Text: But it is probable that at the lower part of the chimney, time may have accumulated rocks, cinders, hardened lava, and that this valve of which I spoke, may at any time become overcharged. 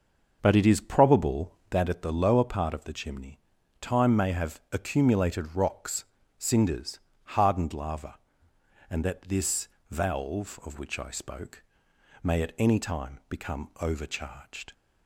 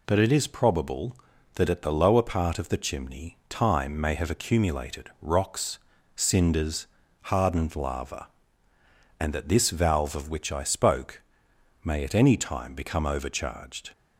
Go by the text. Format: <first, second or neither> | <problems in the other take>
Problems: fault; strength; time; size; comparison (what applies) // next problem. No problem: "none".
second | starts louder than the rest; noticeable; until 1.8 s; 6 dB // pauses between "this" and "valve"; slight; at 9.6 s; 0.20 s long